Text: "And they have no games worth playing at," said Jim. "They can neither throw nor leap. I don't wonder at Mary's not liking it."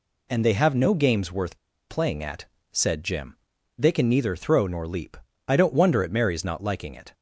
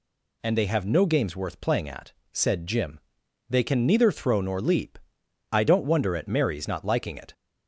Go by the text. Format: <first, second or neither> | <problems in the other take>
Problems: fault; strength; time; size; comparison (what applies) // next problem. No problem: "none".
second | pauses between "worth" and "playing"; slight; at 1.5 s; 0.33 s long